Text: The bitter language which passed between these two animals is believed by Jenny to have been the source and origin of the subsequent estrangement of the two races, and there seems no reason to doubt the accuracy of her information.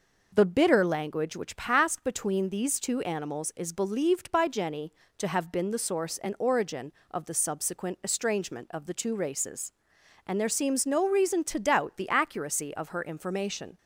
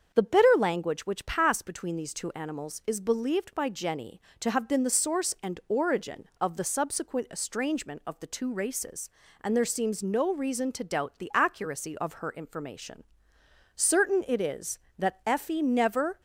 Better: first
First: none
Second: starts louder than the rest; until 1.1 s; 7 dB // goes on to say "Certain it is that Effie never"; strong; from 13.7 s on; 2.4 s long

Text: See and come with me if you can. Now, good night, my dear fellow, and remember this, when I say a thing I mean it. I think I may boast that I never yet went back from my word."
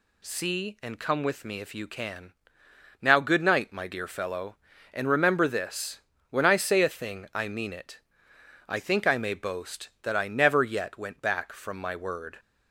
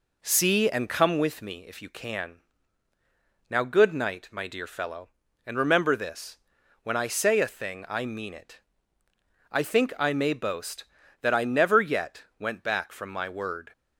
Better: first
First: none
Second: starts louder than the rest; until 1.3 s; 3.5 dB

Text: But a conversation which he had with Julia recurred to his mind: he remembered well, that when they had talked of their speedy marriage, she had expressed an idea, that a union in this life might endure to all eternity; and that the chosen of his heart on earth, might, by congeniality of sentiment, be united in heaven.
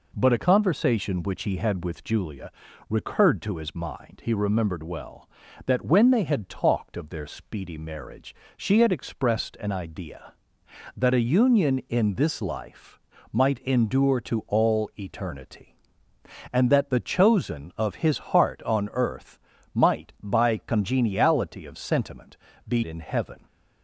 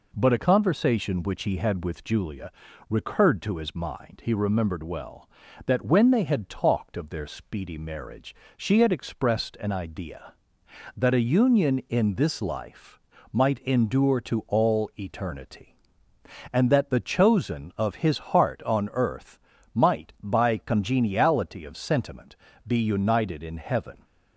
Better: second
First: pauses between "Julia" and "recurred"; at 2.5 s; 0.38 s long // pauses between "life" and "might"; slight; at 13.0 s; 0.32 s long // skips "united"; at 22.8 s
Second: pauses between "Julia" and "recurred"; at 2.5 s; 0.38 s long // pauses between "life" and "might"; slight; at 13.0 s; 0.32 s long

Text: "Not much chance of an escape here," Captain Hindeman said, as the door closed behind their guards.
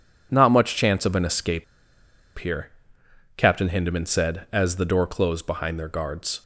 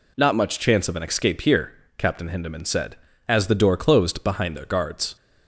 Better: second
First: pauses between "escape" and "here"; noticeable; at 1.6 s; 0.73 s long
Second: none

